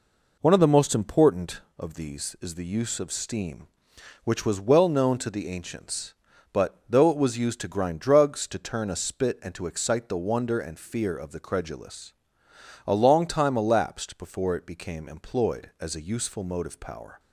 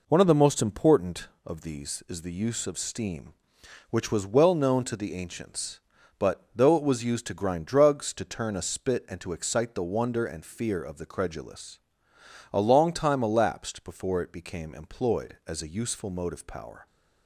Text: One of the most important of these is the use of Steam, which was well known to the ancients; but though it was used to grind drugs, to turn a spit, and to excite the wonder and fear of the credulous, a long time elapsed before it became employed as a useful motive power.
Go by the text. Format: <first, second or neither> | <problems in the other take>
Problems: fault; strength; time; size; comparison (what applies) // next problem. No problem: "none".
neither | none